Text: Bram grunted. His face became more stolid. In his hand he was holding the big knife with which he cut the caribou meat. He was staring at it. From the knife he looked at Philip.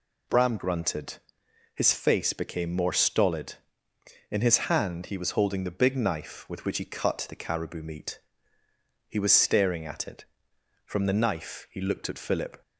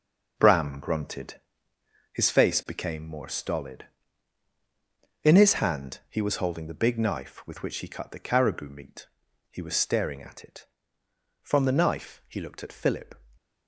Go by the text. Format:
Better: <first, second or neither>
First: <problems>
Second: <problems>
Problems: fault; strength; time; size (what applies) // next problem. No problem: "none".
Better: first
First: none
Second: gets quieter; strong; throughout; 8.5 dB